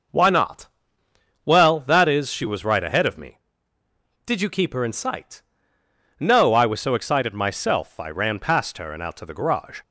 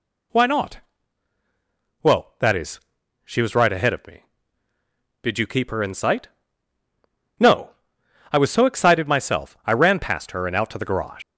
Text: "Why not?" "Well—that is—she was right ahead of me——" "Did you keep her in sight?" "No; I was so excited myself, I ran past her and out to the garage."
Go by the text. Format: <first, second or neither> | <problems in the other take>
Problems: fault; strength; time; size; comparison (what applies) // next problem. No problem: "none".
first | leaves "garage" unfinished; at 11.2 s; 95 ms